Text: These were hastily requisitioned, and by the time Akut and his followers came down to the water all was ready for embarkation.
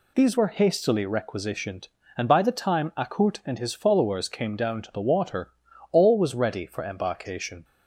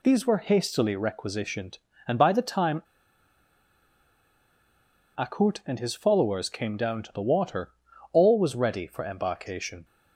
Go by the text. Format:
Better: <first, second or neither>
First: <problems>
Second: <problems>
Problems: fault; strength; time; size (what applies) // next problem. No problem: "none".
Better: first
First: pauses between "water" and "all"; at 5.4 s; 0.40 s long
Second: pauses between "time" and "Akut"; strong; at 2.8 s; 2.3 s long // pauses between "water" and "all"; at 7.7 s; 0.40 s long